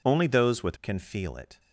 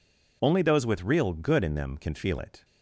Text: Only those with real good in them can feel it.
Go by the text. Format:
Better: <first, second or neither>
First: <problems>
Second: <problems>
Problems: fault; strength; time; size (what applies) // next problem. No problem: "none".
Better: second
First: skips "real good in them"; at 0.7 s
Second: none